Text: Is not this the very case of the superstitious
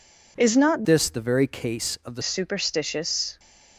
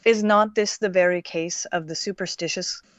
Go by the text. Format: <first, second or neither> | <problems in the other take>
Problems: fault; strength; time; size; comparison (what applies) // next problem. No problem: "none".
second | changes voice from "this" to "the"; from 0.8 to 2.2 s; 1.4 s long